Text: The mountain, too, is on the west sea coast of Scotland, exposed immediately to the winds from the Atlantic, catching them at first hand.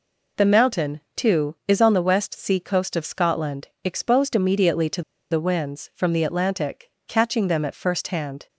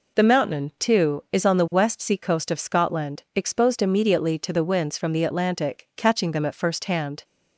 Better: second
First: pauses between "to" and "the"; slight; at 5.0 s; 0.28 s long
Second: none

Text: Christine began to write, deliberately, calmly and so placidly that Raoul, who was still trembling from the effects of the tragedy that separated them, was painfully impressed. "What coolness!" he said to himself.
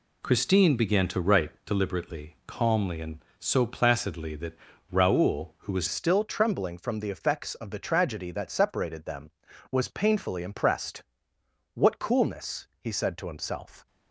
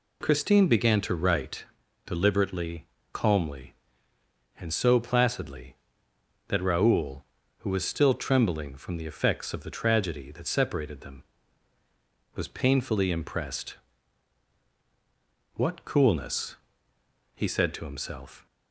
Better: second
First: pauses between "that" and "Raoul"; slight; at 4.5 s; 0.34 s long // changes voice at "still"; from 5.8 s on; 8.0 s long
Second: none

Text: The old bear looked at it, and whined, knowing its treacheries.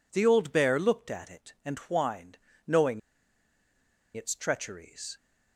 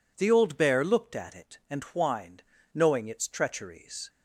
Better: second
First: pauses between "knowing" and "its"; at 2.9 s; 1.1 s long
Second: none

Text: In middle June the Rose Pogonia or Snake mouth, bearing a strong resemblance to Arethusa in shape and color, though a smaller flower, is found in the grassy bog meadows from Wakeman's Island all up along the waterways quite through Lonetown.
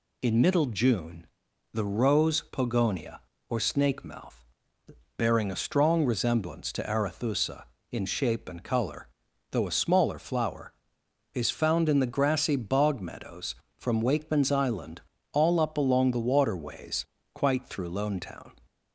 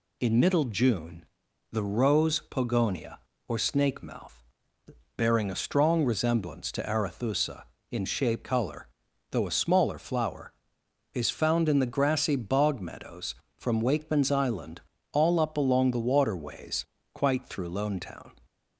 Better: first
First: pauses between "June" and "the"; noticeable; at 1.2 s; 0.48 s long // pauses between "Island" and "all"; slight; at 15.0 s; 0.32 s long // pauses between "waterways" and "quite"; slight; at 17.0 s; 0.30 s long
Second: pauses between "June" and "the"; noticeable; at 1.2 s; 0.48 s long // skips "and"; at 8.4 s // pauses between "Island" and "all"; slight; at 14.8 s; 0.32 s long // pauses between "waterways" and "quite"; slight; at 16.8 s; 0.30 s long

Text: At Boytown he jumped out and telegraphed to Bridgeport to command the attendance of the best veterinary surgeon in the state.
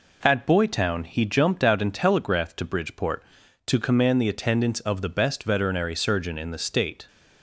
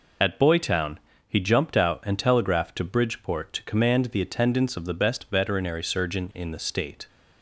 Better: first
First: none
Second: loses the start of "At"; at 0.2 s; 30 ms // pauses between "Boytown" and "he"; slight; at 0.9 s; 0.28 s long

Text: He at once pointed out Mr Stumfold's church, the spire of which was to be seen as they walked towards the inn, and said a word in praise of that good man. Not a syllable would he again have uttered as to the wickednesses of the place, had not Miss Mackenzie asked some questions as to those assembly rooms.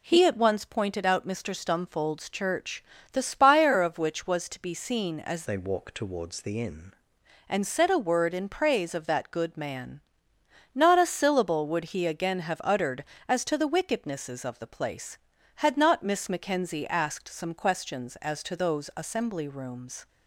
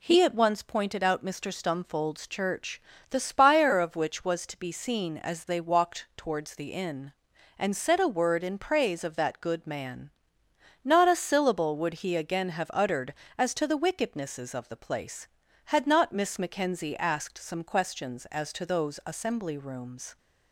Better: second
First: changes voice from "they" to "inn"; from 5.4 to 6.9 s; 1.5 s long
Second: none

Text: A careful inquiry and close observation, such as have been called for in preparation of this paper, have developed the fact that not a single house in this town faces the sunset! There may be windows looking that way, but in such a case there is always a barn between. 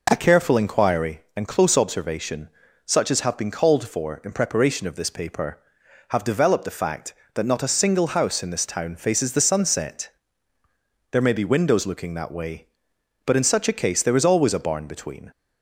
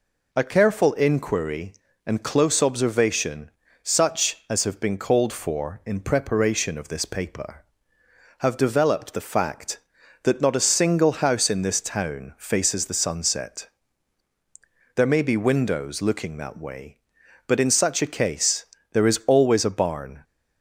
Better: first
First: none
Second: pauses between "case" and "there"; slight; at 18.6 s; 0.30 s long // stops before "between"; at 20.2 s

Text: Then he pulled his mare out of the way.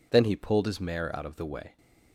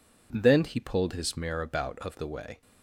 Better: first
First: none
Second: says "about" for "out"; at 1.6 s

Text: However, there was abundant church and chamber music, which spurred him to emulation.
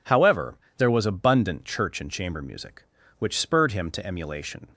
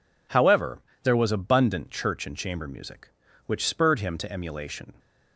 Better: neither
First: none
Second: none

